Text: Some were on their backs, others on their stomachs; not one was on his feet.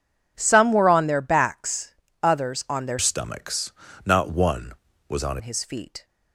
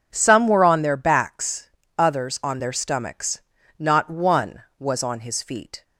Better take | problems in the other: second | changes voice from "stomachs" to "on"; from 2.9 to 5.3 s; 2.4 s long

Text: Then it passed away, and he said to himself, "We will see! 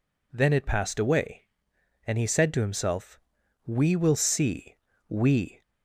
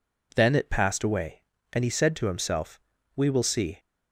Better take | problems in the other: second | goes on to say "We"; from 5.0 s on; 0.54 s long

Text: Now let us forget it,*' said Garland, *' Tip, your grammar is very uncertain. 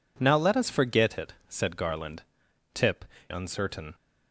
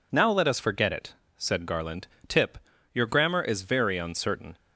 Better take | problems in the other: second | skips "your grammar is very"; at 3.1 s

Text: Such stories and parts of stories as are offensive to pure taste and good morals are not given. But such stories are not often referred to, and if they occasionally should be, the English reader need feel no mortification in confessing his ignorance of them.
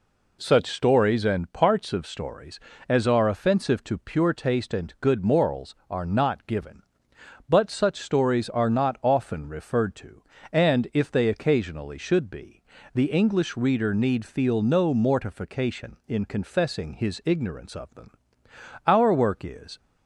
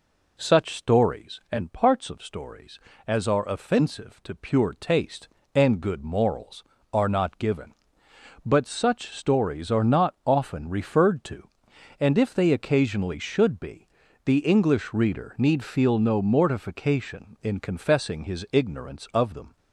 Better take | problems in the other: second | goes on to say "Our work is"; noticeable; from 18.8 s on; 0.92 s long

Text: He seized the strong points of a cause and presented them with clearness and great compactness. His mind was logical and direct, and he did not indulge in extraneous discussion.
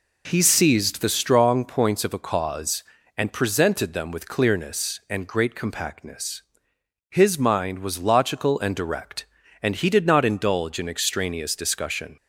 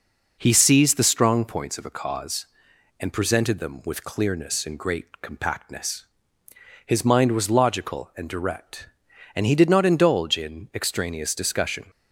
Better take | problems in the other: neither | none

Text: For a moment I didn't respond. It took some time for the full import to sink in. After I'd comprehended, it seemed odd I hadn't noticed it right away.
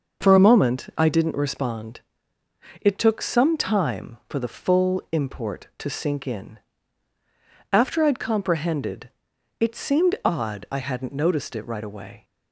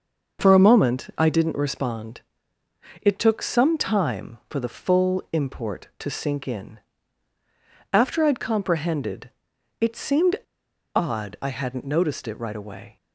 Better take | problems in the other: first | starts louder than the rest; noticeable; until 1.4 s; 6 dB // pauses between "seemed" and "odd"; noticeable; at 10.3 s; 0.58 s long

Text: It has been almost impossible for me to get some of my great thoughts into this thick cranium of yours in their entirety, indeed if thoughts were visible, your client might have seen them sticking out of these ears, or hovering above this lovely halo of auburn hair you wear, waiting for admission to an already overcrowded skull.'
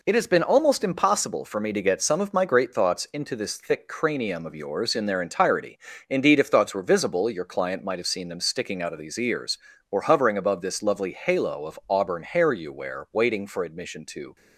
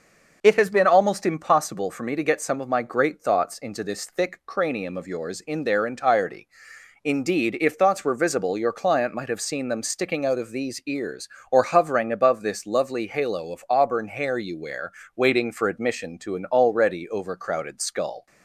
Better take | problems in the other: second | stops before "an already overcrowded skull"; at 14.3 s

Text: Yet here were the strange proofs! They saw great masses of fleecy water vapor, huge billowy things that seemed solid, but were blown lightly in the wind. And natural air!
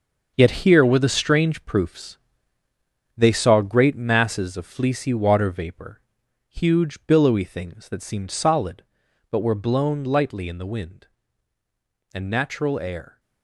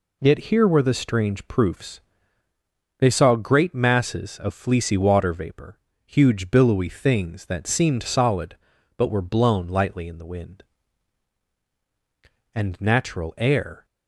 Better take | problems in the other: second | gets quieter; strong; throughout; 9.5 dB

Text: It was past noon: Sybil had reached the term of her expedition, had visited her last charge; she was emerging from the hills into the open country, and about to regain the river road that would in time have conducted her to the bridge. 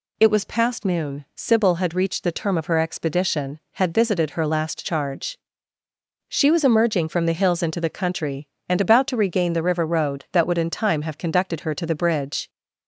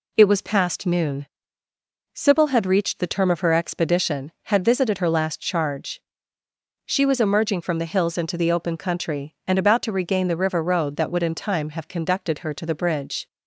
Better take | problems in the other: second | skips "open"; at 7.8 s

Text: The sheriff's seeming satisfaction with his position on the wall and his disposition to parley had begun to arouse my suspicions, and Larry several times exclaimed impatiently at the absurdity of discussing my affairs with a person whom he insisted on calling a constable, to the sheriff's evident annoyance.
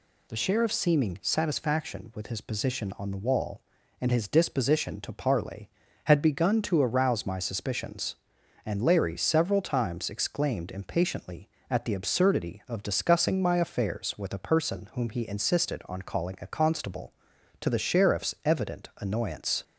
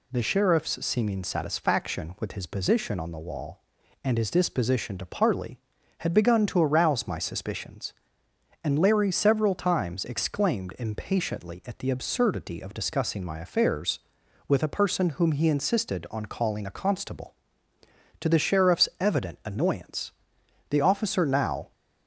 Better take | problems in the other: first | goes on to say "The officer now"; noticeable; from 20.7 s on; 1.0 s long

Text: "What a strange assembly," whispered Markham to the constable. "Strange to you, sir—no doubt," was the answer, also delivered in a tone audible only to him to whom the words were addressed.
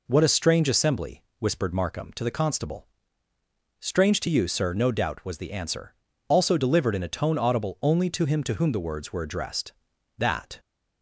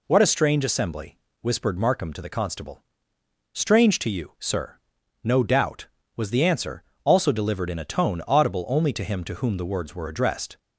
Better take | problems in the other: second | goes on to say "That"; slight; from 10.1 s on; 0.40 s long

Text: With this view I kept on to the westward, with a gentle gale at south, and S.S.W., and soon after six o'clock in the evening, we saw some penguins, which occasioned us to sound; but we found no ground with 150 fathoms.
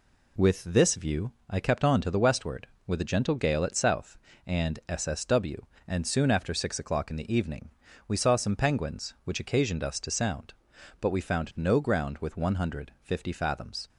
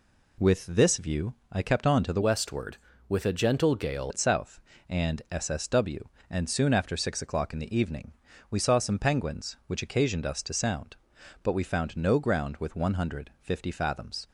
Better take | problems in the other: first | pauses between "view" and "I"; slight; at 1.3 s; 0.18 s long; slight in the first // changes voice from "westward" to "gale"; from 2.2 to 4.1 s; 1.9 s long

